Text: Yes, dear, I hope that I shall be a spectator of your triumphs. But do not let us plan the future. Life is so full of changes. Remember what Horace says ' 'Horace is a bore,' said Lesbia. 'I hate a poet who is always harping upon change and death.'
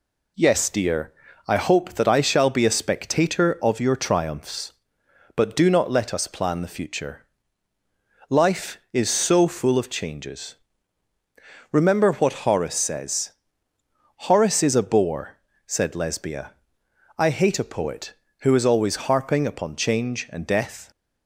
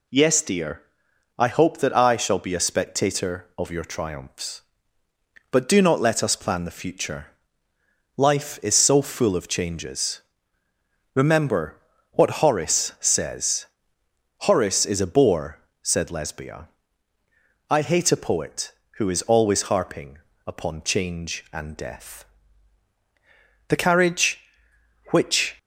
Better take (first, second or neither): first